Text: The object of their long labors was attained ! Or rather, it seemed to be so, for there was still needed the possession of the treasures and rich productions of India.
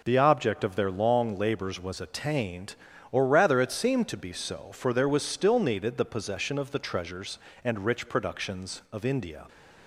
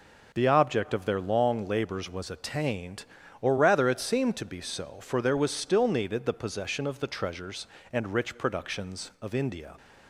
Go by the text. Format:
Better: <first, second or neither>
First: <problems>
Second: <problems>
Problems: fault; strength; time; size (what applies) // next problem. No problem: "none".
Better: neither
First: none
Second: none